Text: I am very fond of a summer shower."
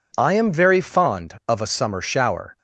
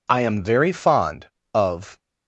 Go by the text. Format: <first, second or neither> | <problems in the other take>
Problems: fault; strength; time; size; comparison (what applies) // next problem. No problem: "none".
first | stops before "a summer shower"; at 1.9 s